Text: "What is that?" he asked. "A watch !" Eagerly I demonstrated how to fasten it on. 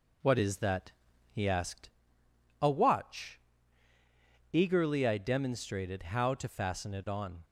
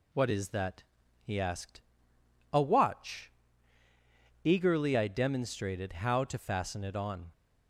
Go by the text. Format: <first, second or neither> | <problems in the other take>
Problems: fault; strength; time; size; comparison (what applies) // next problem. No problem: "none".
second | starts louder than the rest; until 2.0 s; 3.5 dB